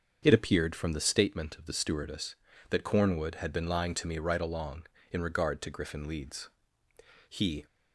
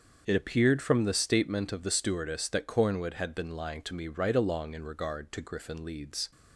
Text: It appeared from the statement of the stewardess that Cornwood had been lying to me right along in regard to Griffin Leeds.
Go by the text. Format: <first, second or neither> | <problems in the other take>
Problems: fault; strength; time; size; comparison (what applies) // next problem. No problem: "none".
second | starts louder than the rest; until 1.2 s; 6.5 dB; also in the second // goes on to say "He"; slight; from 7.2 s on; 0.38 s long